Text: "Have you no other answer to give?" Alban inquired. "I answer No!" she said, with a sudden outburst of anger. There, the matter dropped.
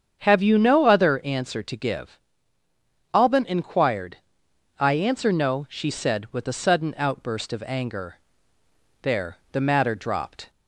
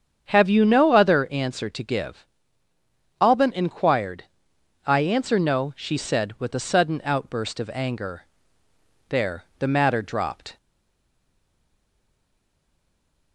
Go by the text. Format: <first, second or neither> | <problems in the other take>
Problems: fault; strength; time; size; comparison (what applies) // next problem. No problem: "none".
first | starts louder than the rest; strong; until 1.3 s; 7.5 dB; strong in the first // stays silent after the last word; strong; from 10.5 s on; 2.8 s long